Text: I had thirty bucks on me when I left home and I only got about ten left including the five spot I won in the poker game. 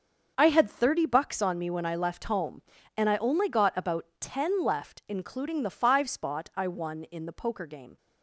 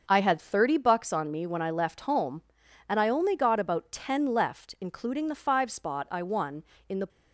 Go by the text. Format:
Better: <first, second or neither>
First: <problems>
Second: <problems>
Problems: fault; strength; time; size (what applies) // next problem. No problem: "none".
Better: first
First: starts louder than the rest; until 1.3 s; 6.5 dB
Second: starts louder than the rest; until 1.0 s; 6.5 dB // stops before "poker game"; at 7.0 s